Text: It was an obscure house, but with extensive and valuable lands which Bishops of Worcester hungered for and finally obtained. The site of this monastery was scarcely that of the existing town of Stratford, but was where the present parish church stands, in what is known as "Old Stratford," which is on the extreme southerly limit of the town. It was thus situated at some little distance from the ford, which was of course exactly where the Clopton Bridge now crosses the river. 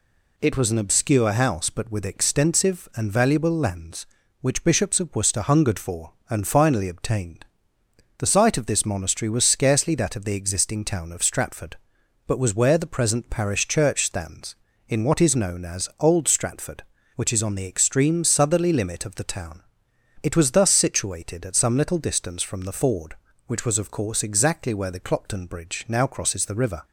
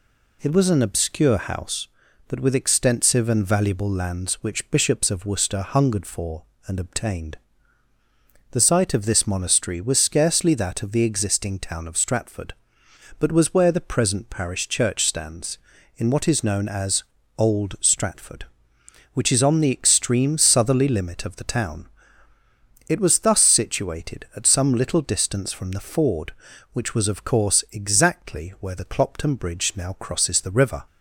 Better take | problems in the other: first | skips "finally"; at 6.7 s // pauses between "as" and "Old"; slight; at 17.0 s; 0.32 s long

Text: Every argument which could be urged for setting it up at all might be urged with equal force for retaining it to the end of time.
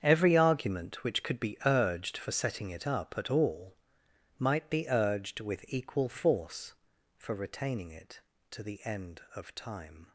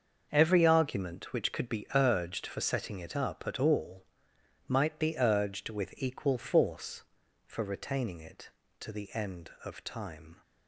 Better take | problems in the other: second | gets quieter; strong; throughout; 14 dB // starts louder than the rest; strong; until 1.0 s; 8 dB; also in the second // pauses between "all" and "might"; noticeable; at 3.7 s; 0.64 s long; noticeable in the second

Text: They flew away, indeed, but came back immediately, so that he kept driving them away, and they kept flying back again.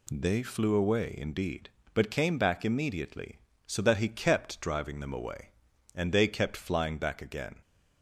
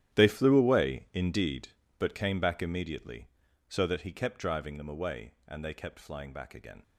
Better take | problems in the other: first | gets quieter; strong; throughout; 15.5 dB

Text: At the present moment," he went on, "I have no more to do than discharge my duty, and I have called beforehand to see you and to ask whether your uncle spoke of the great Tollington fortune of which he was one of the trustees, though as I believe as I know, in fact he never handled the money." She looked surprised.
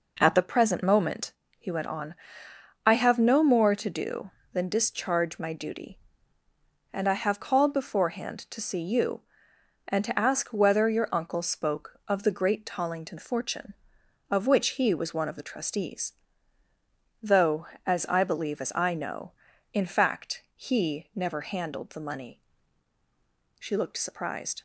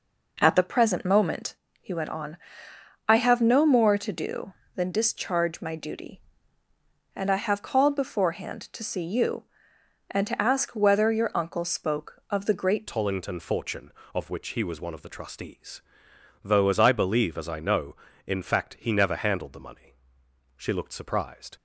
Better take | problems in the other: first | changes voice at "Tollington"; from 12.8 s on; 8.7 s long

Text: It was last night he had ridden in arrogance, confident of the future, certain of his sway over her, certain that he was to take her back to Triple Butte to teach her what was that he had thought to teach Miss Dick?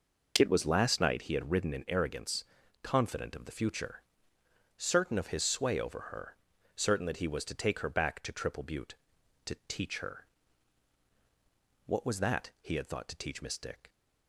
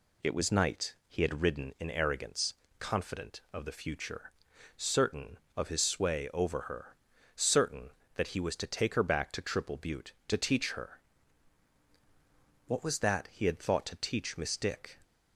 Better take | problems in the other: first | skips "last"; at 0.5 s // pauses between "her" and "what"; strong; at 10.9 s; 1.7 s long; strong in the first

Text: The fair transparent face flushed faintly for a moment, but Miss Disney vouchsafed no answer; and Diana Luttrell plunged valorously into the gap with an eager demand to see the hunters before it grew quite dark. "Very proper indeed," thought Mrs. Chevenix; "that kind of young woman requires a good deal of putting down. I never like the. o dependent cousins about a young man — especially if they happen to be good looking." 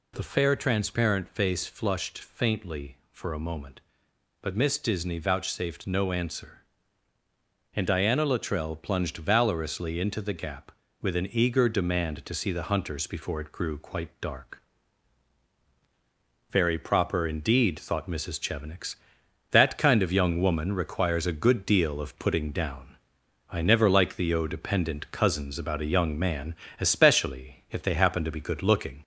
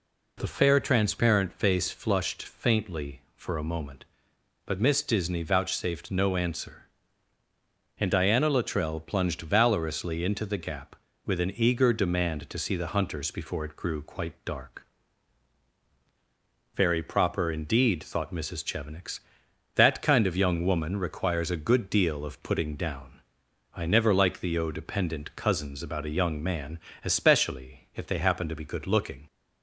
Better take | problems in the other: second | gets louder; slight; throughout; 2 dB

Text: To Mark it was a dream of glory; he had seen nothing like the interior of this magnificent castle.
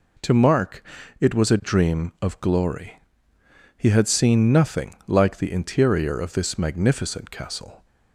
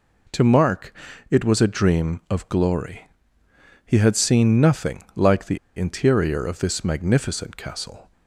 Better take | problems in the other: first | pauses between "Mark" and "it"; slight; at 0.9 s; 0.36 s long; slight in the first // pauses between "the" and "interior"; slight; at 5.5 s; 0.18 s long

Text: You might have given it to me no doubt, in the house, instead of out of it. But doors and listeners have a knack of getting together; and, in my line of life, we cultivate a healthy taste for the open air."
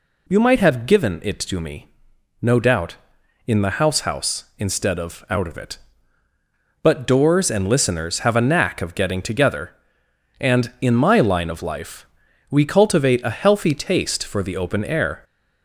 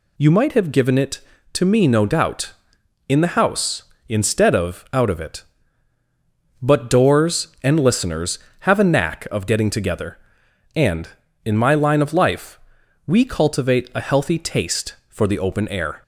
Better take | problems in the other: second | pauses between "me" and "no"; noticeable; at 1.8 s; 0.54 s long // says "house" twice; at 4.0 s

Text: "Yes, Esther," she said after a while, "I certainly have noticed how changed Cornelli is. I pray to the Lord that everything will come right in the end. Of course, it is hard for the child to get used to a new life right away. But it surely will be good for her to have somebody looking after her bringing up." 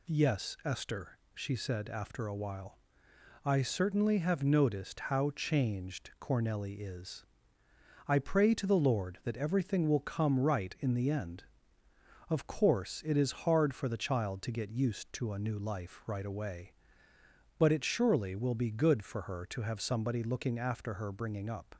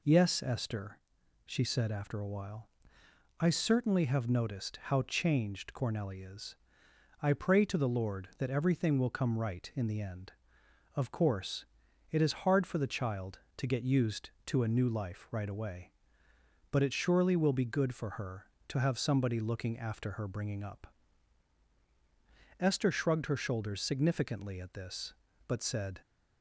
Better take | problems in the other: first | goes on to say "Esther shrugged her shoulders significantly at this but said"; strong; from 22.5 s on; 3.4 s long

